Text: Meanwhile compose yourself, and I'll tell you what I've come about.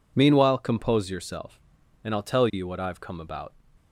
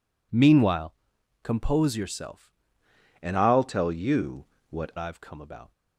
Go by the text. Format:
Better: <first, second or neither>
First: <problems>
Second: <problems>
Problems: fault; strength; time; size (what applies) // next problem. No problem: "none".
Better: first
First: none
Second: pauses between "Meanwhile" and "compose"; noticeable; at 0.9 s; 0.48 s long // changes voice from "and" to "what"; from 3.2 to 4.9 s; 1.7 s long // pauses between "you" and "what"; slight; at 4.4 s; 0.26 s long